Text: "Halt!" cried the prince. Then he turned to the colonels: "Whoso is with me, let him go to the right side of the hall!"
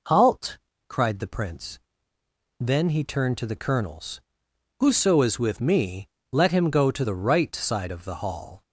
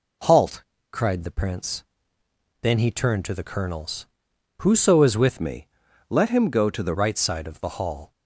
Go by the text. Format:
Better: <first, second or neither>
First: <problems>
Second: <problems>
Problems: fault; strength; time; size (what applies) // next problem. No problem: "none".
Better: first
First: none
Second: changes voice from "me" to "the"; from 5.3 to 6.9 s; 1.6 s long